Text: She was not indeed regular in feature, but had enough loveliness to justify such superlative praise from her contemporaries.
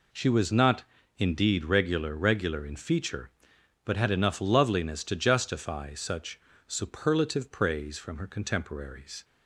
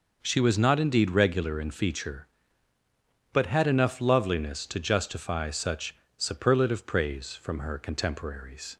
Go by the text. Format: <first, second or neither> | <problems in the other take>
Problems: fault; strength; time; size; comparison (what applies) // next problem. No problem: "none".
second | pauses between "not" and "indeed"; slight; at 0.8 s; 0.32 s long // says "regular" twice; at 2.1 s // pauses between "such" and "superlative"; slight; at 6.3 s; 0.28 s long; slight in the second